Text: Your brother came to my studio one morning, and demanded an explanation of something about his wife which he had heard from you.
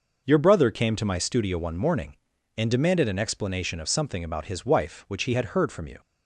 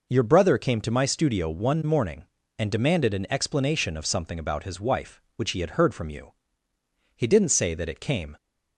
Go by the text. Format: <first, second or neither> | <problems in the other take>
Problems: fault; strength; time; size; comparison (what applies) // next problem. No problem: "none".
first | goes on to say "He didn't say that it came"; noticeable; from 7.1 s on; 1.2 s long